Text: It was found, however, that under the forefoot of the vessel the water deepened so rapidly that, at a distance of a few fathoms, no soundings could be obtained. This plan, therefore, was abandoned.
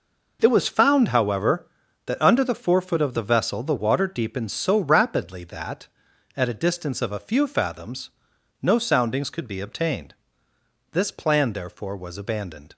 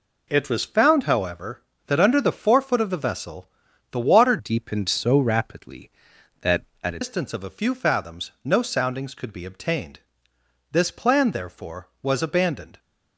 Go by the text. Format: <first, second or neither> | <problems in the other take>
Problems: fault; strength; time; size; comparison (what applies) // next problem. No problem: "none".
first | pauses between "vessel" and "the"; at 3.4 s; 0.42 s long // changes voice from "deepened" to "a"; from 4.3 to 6.9 s; 2.6 s long